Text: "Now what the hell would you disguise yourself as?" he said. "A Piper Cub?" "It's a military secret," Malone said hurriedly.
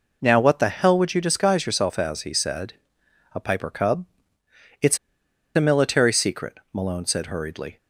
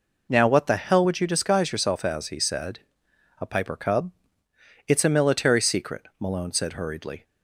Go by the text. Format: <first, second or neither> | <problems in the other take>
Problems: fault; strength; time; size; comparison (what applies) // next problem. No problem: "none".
second | pauses between "It's" and "a"; noticeable; at 4.9 s; 0.57 s long